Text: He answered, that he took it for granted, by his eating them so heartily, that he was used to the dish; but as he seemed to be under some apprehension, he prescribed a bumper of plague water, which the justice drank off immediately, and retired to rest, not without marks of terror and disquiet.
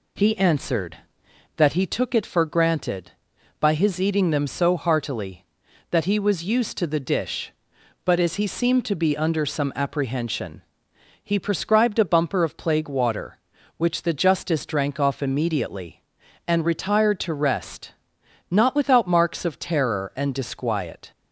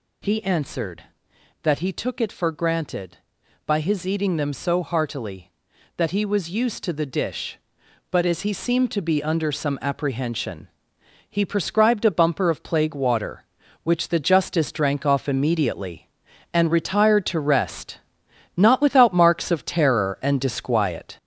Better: first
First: none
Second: gets louder; noticeable; throughout; 4.5 dB

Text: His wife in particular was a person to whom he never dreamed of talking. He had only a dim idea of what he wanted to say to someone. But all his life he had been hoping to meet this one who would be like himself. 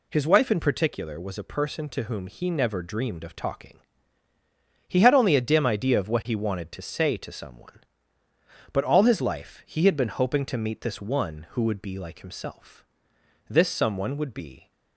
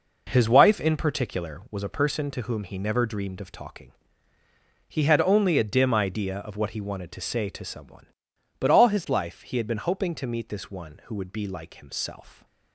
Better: second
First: goes on to say "This someone would be"; noticeable; from 13.4 s on; 1.2 s long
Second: none

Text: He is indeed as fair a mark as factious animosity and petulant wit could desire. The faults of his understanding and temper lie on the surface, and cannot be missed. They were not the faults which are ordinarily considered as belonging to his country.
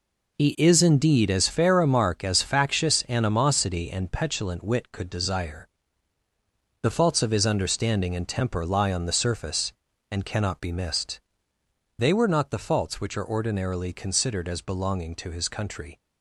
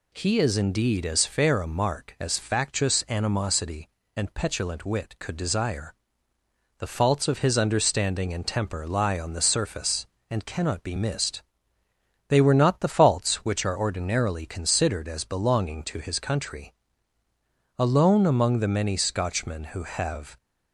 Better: first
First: none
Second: goes on to say "Alone among the many Scotchmen who have"; strong; from 17.7 s on; 2.5 s long

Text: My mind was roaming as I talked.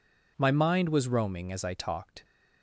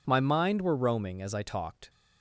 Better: first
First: none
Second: says "were" for "was"; at 0.6 s

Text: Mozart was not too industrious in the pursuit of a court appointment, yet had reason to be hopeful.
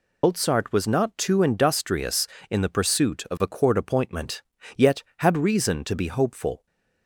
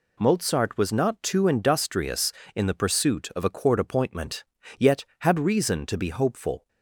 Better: second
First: loses the start of "Mozart"; at 0.2 s; 90 ms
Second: none

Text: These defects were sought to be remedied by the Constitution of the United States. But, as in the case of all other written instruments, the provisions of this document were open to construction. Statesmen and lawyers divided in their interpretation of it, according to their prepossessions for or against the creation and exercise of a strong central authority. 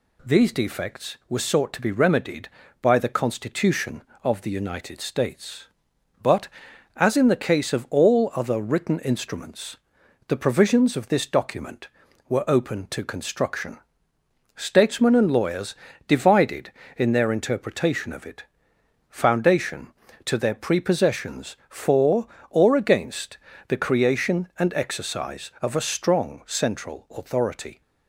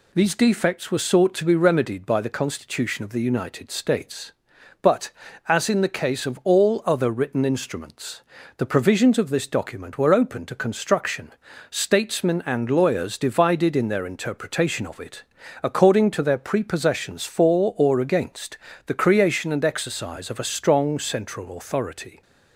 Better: second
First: pauses between "lawyers" and "divided"; slight; at 15.7 s; 0.34 s long // says "foundation" for "according"; at 19.0 s // pauses between "against" and "the"; slight; at 23.3 s; 0.32 s long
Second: pauses between "against" and "the"; slight; at 18.5 s; 0.30 s long

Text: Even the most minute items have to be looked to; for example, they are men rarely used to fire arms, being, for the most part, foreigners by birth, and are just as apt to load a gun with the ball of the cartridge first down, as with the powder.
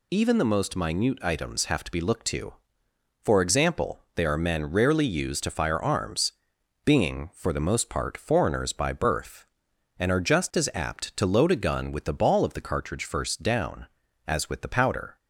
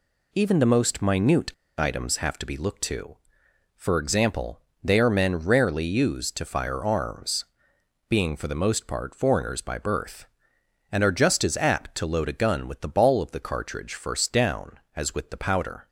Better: first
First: none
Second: pauses between "minute" and "items"; slight; at 1.5 s; 0.26 s long

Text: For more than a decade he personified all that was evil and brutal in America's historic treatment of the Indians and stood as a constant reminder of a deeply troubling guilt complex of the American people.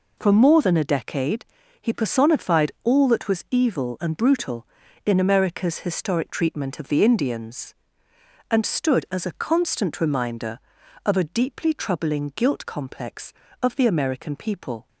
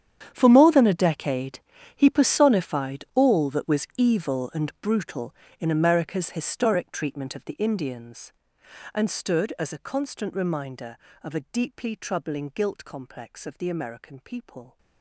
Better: first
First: pauses between "decade" and "he"; slight; at 1.4 s; 0.34 s long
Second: gets quieter; strong; throughout; 18 dB // pauses between "decade" and "he"; slight; at 1.5 s; 0.36 s long

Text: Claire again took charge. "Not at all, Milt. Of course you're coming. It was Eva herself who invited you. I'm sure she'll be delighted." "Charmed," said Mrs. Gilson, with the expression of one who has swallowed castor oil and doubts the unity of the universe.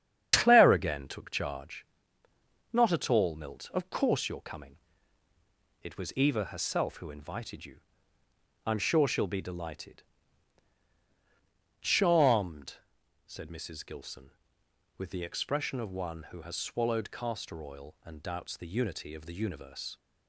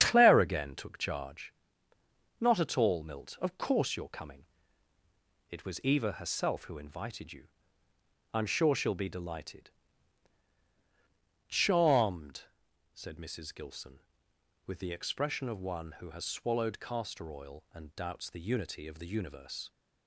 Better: neither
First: starts louder than the rest; strong; until 1.3 s; 8.5 dB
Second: starts louder than the rest; strong; until 1.0 s; 8.5 dB

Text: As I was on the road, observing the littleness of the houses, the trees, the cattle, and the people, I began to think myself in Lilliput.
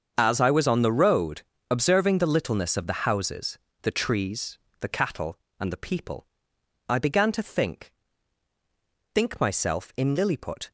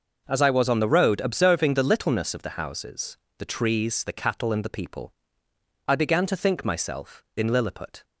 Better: second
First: starts louder than the rest; strong; until 1.1 s; 7 dB // says "think" twice; at 9.1 s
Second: none

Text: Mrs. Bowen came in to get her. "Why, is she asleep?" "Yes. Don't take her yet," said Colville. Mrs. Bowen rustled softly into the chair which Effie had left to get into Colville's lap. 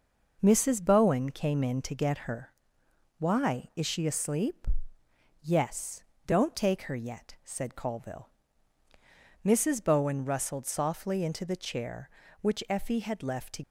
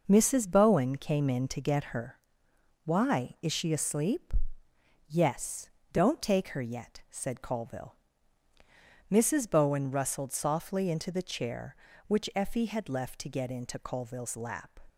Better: second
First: stops before "get into Colville's lap"; at 13.6 s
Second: none

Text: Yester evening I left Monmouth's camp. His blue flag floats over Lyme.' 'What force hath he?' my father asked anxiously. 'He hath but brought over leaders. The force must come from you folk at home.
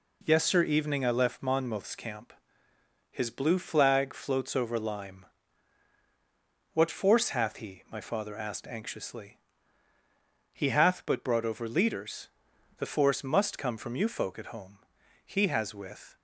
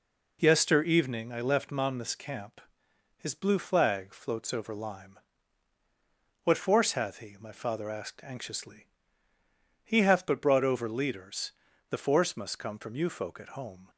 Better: second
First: goes on to say "He has with"; noticeable; from 15.2 s on; 0.90 s long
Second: none

